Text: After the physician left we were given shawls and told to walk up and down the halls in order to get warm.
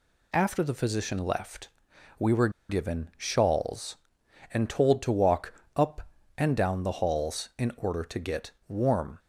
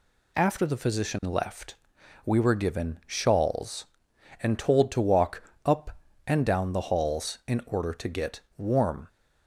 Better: second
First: pauses between "left" and "we"; noticeable; at 1.6 s; 0.50 s long // pauses between "were" and "given"; slight; at 2.4 s; 0.19 s long // pauses between "walk" and "up"; slight; at 5.5 s; 0.22 s long // pauses between "get" and "warm"; slight; at 8.5 s; 0.18 s long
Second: pauses between "left" and "we"; noticeable; at 1.7 s; 0.50 s long // pauses between "walk" and "up"; slight; at 5.4 s; 0.22 s long // pauses between "get" and "warm"; slight; at 8.3 s; 0.18 s long

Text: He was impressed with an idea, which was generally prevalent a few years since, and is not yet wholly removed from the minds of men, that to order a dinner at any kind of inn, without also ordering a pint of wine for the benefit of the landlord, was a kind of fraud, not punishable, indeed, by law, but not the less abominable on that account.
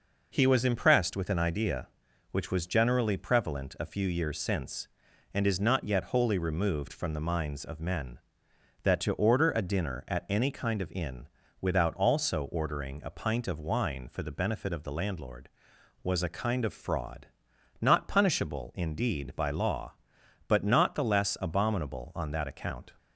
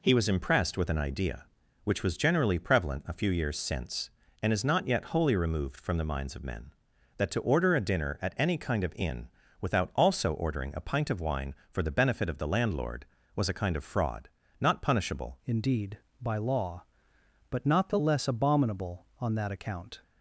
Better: first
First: none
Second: changes voice at "indeed"; from 15.4 s on; 4.6 s long

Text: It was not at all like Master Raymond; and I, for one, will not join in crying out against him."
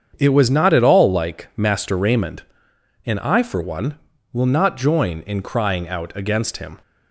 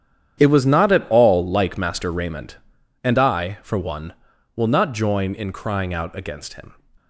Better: first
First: starts louder than the rest; strong; until 1.1 s; 7.5 dB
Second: gets quieter; strong; throughout; 14 dB // starts louder than the rest; strong; until 1.4 s; 9.5 dB

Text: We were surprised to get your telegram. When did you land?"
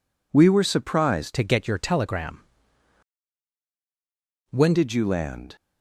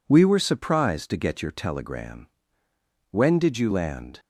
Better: second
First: changes voice from "to" to "When"; from 1.3 to 4.7 s; 3.4 s long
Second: none

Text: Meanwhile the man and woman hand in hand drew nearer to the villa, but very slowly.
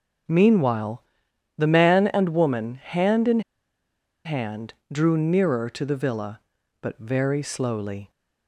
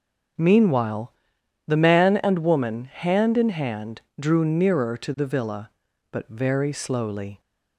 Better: second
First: starts louder than the rest; until 1.8 s; 6.5 dB // pauses between "Meanwhile" and "the"; noticeable; at 1.0 s; 0.56 s long // pauses between "in" and "hand"; noticeable; at 3.3 s; 0.85 s long // pauses between "hand" and "drew"; slight; at 4.7 s; 0.18 s long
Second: starts louder than the rest; until 1.9 s; 6.5 dB // pauses between "Meanwhile" and "the"; noticeable; at 1.1 s; 0.56 s long // pauses between "hand" and "drew"; slight; at 4.0 s; 0.18 s long

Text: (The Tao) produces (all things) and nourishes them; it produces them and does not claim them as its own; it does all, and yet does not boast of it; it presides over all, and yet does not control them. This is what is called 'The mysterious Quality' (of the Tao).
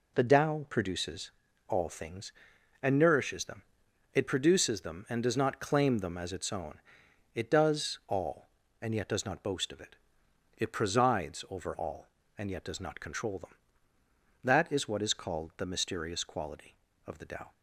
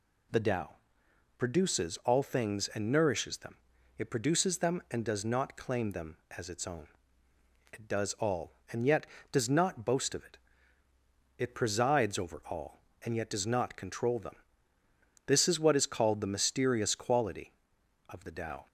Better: second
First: says "That" for "This"; at 14.4 s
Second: none

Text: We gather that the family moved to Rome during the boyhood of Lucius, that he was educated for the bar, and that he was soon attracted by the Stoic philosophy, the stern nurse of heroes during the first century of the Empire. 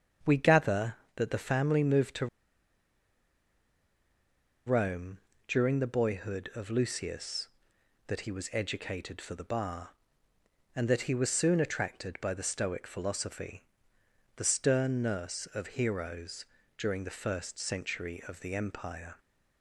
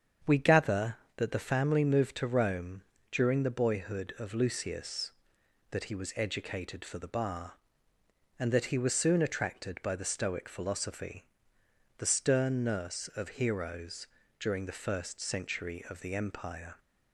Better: second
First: starts louder than the rest; strong; until 1.4 s; 7.5 dB // pauses between "to" and "Rome"; strong; at 2.2 s; 2.3 s long // pauses between "Rome" and "during"; slight; at 5.1 s; 0.28 s long // pauses between "heroes" and "during"; slight; at 16.4 s; 0.32 s long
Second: starts louder than the rest; strong; until 1.4 s; 7.5 dB // pauses between "Rome" and "during"; slight; at 2.8 s; 0.28 s long // pauses between "heroes" and "during"; slight; at 14.0 s; 0.32 s long

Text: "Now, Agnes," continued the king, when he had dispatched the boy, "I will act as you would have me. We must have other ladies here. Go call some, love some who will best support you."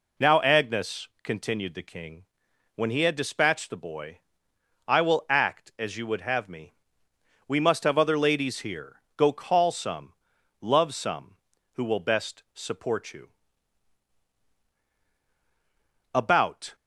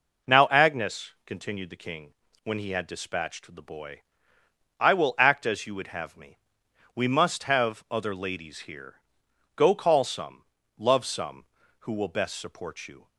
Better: second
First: goes on to say "About"; noticeable; from 16.1 s on; 0.62 s long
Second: none

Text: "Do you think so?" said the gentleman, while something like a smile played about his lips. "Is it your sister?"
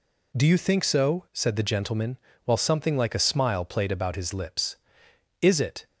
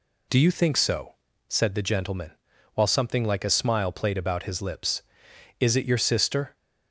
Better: second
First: stops before "your sister"; at 5.8 s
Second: none

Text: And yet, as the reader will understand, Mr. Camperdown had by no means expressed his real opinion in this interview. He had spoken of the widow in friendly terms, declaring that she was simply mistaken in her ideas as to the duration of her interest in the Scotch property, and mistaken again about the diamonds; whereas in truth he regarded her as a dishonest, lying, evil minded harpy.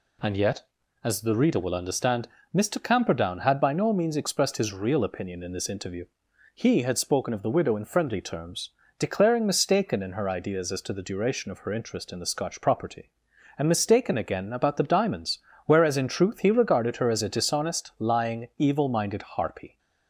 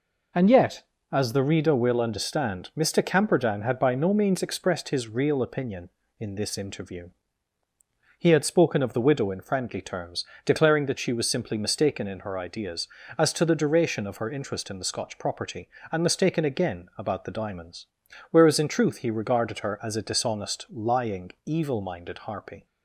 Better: second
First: skips "that she was simply"; at 9.4 s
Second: none

